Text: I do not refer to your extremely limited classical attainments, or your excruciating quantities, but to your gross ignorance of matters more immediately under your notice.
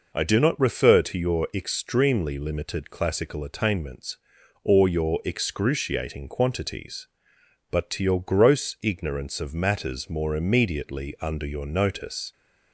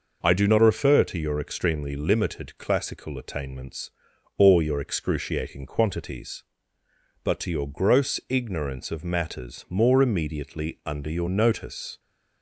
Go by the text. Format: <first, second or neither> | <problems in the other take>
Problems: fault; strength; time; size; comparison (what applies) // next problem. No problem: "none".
neither | none